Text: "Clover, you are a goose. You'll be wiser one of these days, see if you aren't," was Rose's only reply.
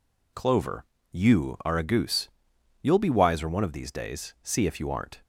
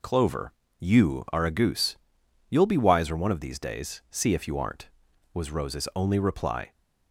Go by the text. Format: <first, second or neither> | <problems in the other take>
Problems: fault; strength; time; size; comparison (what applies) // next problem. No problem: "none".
second | stops before "was Rose's only reply"; at 5.2 s